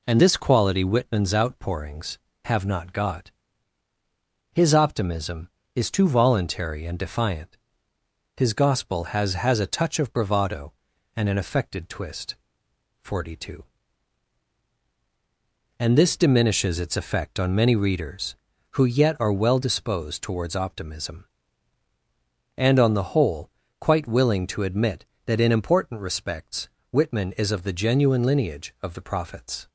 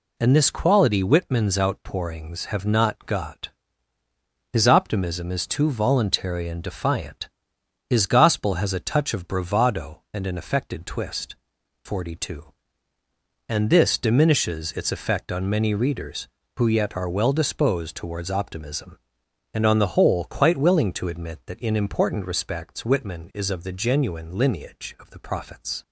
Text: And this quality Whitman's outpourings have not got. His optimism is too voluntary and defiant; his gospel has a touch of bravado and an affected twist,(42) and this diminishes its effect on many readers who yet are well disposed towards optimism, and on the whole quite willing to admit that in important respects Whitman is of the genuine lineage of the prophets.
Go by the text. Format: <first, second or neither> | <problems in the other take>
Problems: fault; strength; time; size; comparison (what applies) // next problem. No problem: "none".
second | says "has" twice; at 9.3 s // pauses between "whole" and "quite"; slight; at 23.4 s; 0.30 s long // pauses between "respects" and "Whitman"; slight; at 26.6 s; 0.20 s long